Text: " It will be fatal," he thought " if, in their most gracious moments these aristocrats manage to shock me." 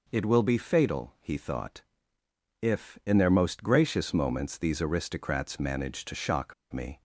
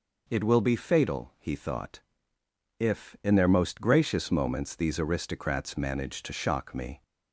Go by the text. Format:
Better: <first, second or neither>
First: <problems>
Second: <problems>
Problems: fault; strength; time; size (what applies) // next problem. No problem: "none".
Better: second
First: pauses between "shock" and "me"; slight; at 6.5 s; 0.19 s long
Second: none